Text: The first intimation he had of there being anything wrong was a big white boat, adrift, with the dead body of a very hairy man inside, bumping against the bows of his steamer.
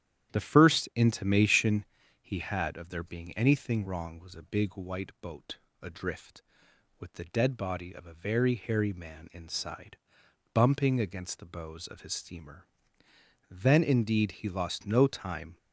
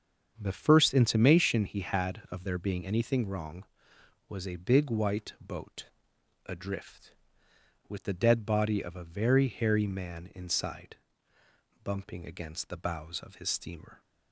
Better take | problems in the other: second | starts louder than the rest; strong; until 1.4 s; 10.5 dB; also in the second // pauses between "intimation" and "he"; slight; at 1.8 s; 0.36 s long // goes on to say "Then indeed he lost no time"; strong; from 13.5 s on; 2.0 s long

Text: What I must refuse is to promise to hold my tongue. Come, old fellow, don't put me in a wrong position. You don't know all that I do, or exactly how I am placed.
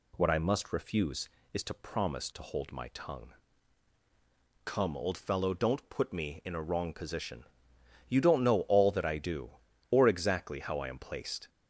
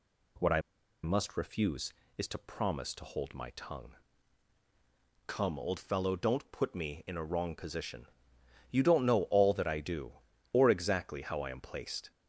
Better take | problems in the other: first | pauses between "I" and "must"; at 0.6 s; 0.42 s long

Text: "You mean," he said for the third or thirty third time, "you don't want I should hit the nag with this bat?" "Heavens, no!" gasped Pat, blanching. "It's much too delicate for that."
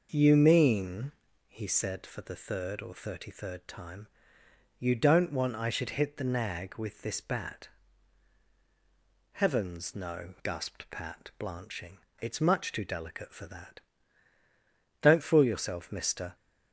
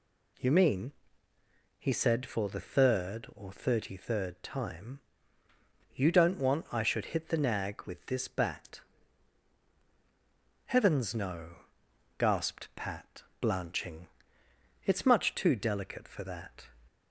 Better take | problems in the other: second | goes on to say "Don't fool yourself mister"; from 15.0 s on; 1.3 s long

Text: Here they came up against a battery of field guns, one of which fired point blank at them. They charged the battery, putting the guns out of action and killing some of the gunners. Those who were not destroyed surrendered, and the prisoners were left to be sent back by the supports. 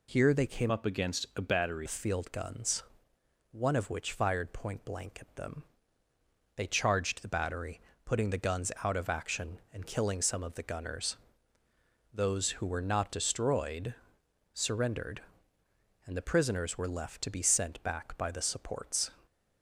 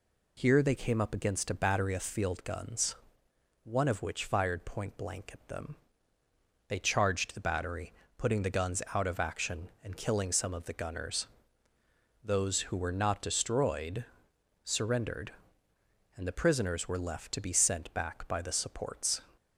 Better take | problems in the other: second | changes voice from "up" to "battery"; from 0.6 to 1.8 s; 1.2 s long // pauses between "destroyed" and "surrendered"; noticeable; at 13.9 s; 0.60 s long; noticeable in the second

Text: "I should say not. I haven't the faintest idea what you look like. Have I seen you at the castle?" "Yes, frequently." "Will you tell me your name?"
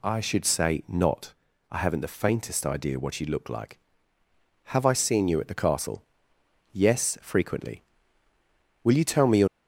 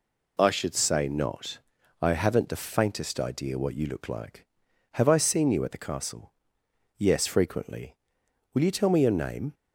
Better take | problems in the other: second | stops before "name"; at 9.4 s

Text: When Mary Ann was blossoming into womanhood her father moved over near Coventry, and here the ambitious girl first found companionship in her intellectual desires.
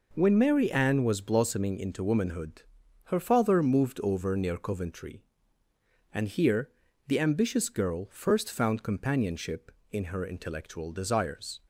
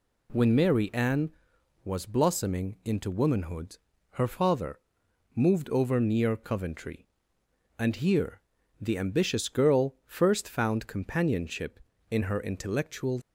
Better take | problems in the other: first | pauses between "womanhood" and "her"; slight; at 3.7 s; 0.32 s long; also in the first // pauses between "father" and "moved"; noticeable; at 4.7 s; 0.56 s long // pauses between "here" and "the"; at 8.3 s; 0.40 s long; also in the first // stops before "desires"; at 13.2 s

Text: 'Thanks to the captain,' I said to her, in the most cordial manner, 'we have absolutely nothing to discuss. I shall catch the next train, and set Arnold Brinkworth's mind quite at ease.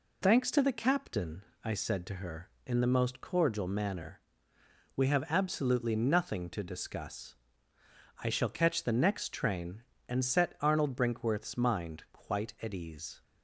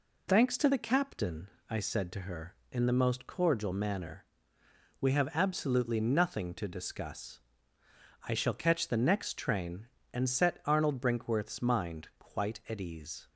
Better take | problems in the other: neither | none

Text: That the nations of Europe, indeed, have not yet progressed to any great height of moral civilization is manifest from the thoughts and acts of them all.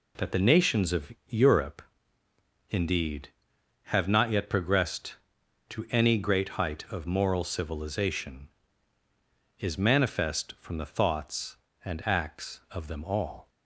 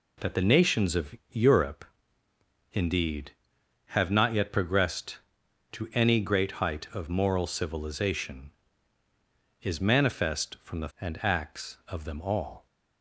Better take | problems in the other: first | pauses between "of" and "Europe"; slight; at 1.1 s; 0.16 s long; slight in the first // skips "thoughts"; at 10.9 s

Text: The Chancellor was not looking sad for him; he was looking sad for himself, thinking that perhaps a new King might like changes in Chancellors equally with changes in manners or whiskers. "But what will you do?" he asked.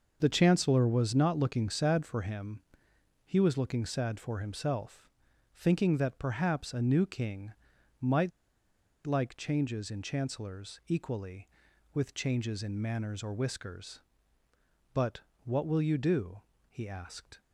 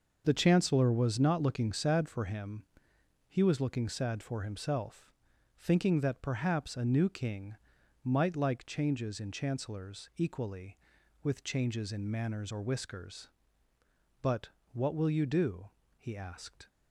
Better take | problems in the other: second | starts louder than the rest; noticeable; until 1.2 s; 6 dB; also in the second // pauses between "King" and "might"; noticeable; at 7.5 s; 0.46 s long; noticeable in the second // pauses between "might" and "like"; noticeable; at 8.3 s; 0.74 s long // pauses between "But" and "what"; slight; at 15.1 s; 0.24 s long; slight in the second

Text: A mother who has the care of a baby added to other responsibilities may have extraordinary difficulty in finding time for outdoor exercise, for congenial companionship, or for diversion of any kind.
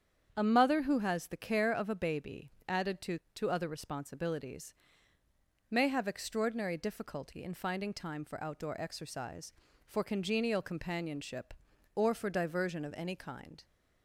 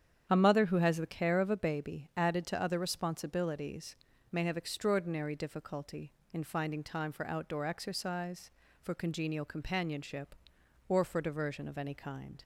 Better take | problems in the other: second | starts louder than the rest; strong; until 1.3 s; 8 dB; strong in the second // pauses between "baby" and "added"; slight; at 2.5 s; 0.18 s long // says "to" twice; at 3.3 s // pauses between "responsibilities" and "may"; noticeable; at 4.7 s; 0.96 s long; also in the second

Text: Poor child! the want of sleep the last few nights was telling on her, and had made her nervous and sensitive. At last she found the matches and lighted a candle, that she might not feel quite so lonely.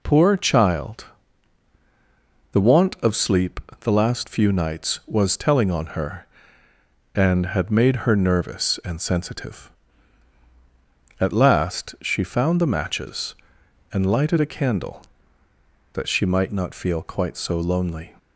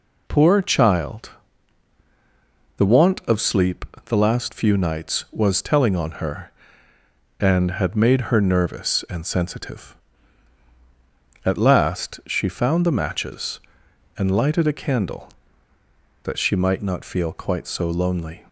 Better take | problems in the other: neither | pauses between "sleep" and "the"; slight; the same in both

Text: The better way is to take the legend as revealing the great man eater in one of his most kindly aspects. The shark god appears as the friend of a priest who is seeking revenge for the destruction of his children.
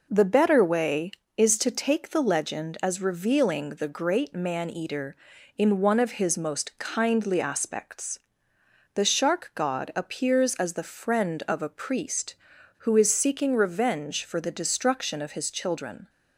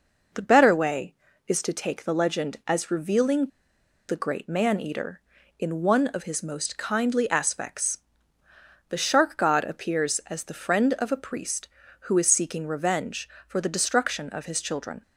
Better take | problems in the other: first | pauses between "revealing" and "the"; noticeable; at 3.4 s; 0.61 s long

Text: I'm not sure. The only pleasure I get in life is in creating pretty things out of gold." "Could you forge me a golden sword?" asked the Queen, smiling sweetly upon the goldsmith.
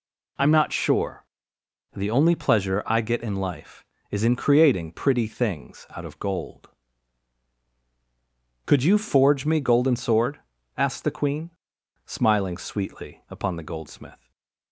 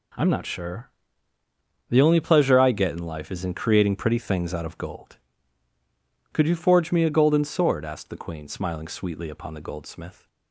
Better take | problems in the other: second | skips "a"; at 9.5 s // stays silent after the last word; slight; from 14.1 s on; 0.6 s long

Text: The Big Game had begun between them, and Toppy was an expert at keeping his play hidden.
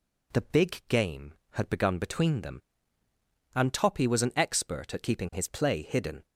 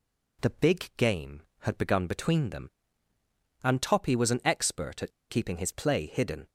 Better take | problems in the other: first | pauses between "at" and "keeping"; slight; at 5.1 s; 0.20 s long

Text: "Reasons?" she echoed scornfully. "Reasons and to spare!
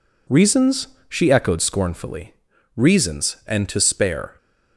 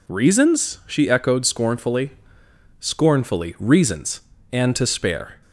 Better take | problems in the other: first | says "scornfully" twice; at 2.7 s

